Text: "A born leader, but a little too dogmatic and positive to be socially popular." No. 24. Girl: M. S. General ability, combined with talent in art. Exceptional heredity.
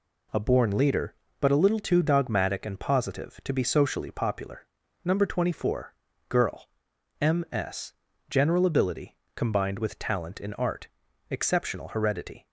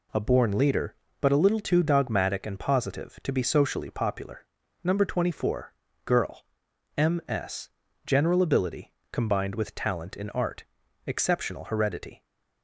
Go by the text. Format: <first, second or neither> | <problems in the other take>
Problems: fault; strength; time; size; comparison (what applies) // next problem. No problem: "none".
neither | pauses between "S" and "General"; the same in both